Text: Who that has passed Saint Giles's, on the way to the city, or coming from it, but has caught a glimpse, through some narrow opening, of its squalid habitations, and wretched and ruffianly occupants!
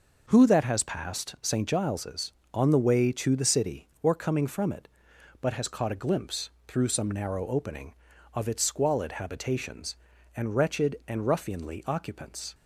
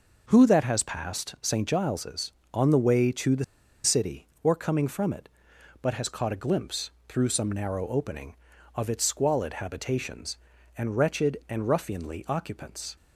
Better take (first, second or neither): first